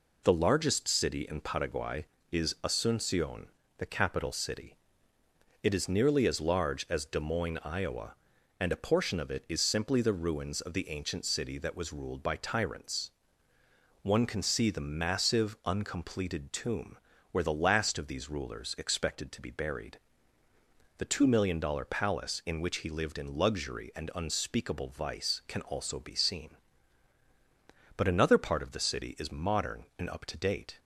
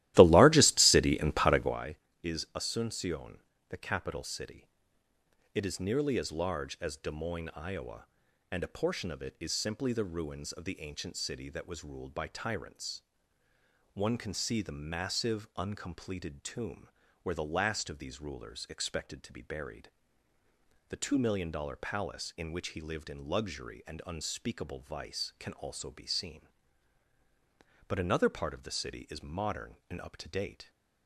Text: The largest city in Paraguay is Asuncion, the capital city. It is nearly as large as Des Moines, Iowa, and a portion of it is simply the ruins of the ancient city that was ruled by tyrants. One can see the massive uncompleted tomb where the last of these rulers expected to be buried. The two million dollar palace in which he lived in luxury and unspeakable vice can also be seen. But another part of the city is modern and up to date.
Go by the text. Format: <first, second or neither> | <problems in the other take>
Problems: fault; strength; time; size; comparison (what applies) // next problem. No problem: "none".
first | starts louder than the rest; strong; until 1.9 s; 15.5 dB // pauses between "tomb" and "where"; slight; at 16.8 s; 0.34 s long; slight in the first